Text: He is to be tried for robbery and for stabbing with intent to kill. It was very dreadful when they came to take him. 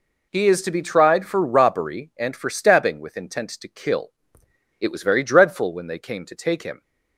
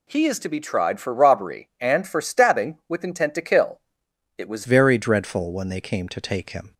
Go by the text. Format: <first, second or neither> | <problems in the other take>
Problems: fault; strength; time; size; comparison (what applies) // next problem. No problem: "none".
first | changes voice at "very"; from 4.6 s on; 2.1 s long